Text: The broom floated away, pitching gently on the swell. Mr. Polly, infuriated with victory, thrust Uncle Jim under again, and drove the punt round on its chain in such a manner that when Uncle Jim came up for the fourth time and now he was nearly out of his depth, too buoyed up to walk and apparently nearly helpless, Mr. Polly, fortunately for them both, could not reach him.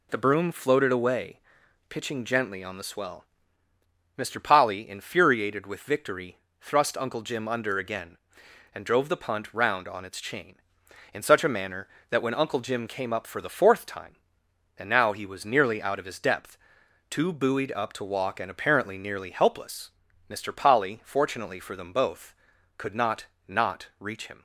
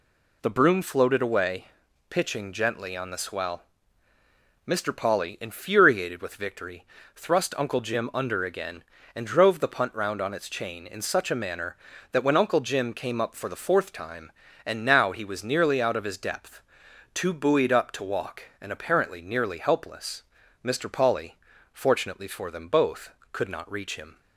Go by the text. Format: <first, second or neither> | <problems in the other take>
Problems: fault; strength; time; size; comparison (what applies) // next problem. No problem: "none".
second | says "not" twice; at 23.4 s